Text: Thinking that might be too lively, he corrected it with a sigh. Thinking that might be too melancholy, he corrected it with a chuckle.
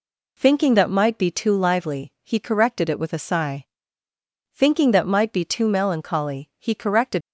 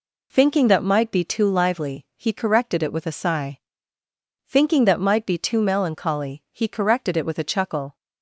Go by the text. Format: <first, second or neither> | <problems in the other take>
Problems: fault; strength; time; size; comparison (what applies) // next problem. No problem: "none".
second | stops before "it with a chuckle"; at 7.2 s